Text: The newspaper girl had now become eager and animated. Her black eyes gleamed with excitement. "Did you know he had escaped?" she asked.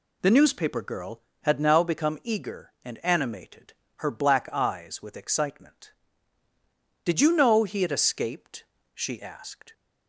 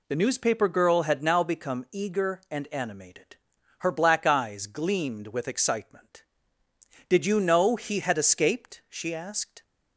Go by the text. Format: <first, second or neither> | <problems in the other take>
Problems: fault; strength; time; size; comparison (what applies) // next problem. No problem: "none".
second | skips "gleamed"; at 5.0 s